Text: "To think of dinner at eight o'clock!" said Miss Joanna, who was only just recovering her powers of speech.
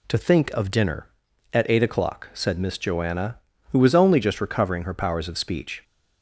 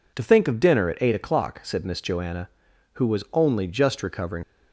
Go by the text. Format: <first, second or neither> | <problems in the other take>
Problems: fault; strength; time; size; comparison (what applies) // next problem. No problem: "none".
first | stops before "her powers of speech"; at 4.4 s